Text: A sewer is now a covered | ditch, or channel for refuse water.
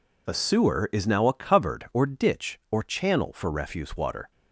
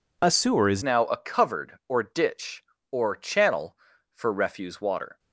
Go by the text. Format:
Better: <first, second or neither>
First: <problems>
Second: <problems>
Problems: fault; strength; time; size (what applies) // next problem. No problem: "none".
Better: first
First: none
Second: changes voice at "now"; from 0.8 s on; 4.3 s long